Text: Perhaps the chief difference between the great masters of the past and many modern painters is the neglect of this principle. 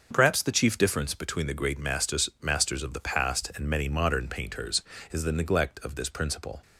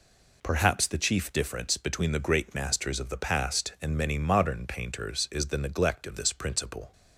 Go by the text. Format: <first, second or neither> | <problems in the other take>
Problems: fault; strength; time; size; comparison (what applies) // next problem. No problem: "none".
second | starts louder than the rest; until 1.1 s; 6.5 dB // says "masters" twice; at 2.4 s